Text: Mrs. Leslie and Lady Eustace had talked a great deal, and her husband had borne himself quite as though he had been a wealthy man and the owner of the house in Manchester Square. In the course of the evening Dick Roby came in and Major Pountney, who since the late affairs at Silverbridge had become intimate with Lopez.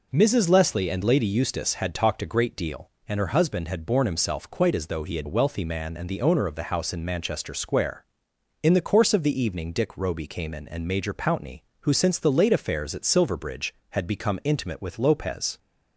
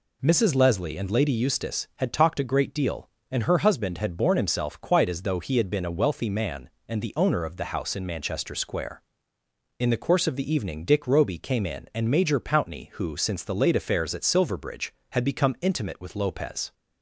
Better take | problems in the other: second | skips "been"; at 5.2 s

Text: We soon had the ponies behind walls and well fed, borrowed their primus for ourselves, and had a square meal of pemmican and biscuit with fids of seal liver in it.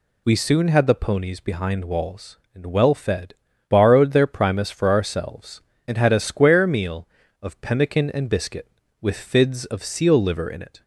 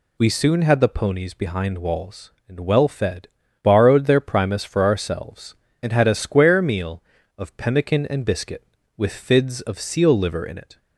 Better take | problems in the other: neither | none

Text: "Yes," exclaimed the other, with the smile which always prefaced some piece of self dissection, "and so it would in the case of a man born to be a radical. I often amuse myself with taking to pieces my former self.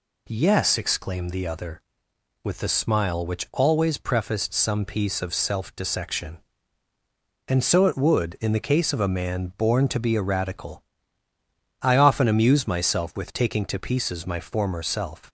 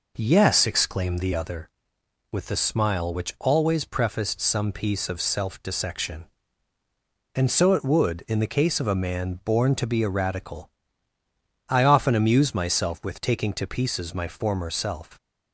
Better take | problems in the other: first | starts louder than the rest; noticeable; until 1.6 s; 5 dB

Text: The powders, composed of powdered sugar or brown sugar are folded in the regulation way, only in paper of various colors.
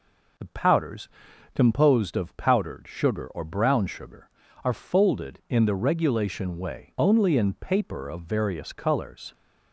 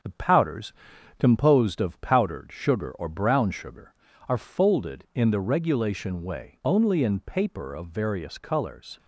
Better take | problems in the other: first | gets quieter; throughout; 3.5 dB

